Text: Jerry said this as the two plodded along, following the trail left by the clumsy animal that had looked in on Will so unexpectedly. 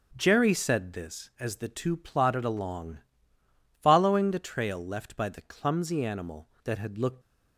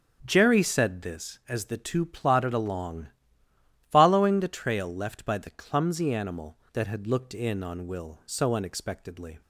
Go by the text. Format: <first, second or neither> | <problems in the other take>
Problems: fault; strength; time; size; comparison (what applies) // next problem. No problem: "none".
second | starts louder than the rest; until 1.1 s; 6.5 dB; strong in the second // stops before "in on Will so unexpectedly"; at 7.2 s